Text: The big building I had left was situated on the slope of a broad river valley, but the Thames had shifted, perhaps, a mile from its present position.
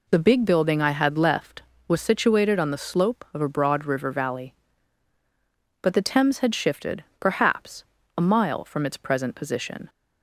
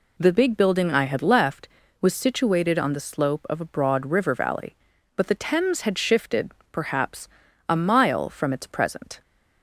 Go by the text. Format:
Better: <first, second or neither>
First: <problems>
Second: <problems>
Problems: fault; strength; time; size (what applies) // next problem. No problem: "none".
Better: first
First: none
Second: stops before "position"; at 9.2 s